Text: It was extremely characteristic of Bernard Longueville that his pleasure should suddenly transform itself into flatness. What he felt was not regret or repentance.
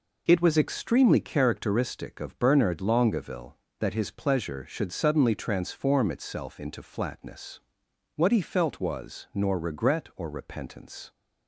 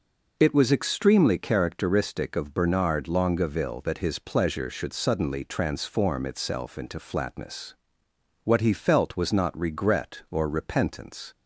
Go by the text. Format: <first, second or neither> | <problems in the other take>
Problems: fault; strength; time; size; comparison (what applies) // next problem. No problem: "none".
second | says "nor" for "not"; at 9.3 s